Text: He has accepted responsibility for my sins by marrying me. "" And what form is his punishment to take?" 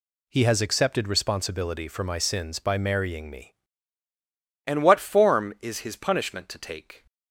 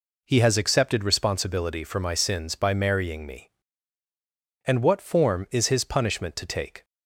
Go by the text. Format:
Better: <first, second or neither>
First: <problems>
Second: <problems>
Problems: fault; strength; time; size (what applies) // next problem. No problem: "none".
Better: second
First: changes voice at "And"; from 4.6 s on; 2.4 s long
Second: none